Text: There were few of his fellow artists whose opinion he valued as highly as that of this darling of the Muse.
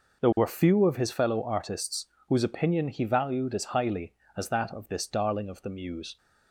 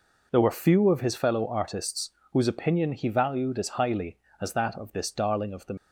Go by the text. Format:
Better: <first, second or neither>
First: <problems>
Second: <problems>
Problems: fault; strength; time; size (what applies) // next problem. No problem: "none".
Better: first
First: pauses between "artists" and "whose"; slight; at 2.0 s; 0.24 s long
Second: pauses between "artists" and "whose"; slight; at 2.0 s; 0.24 s long // stops before "Muse"; at 5.7 s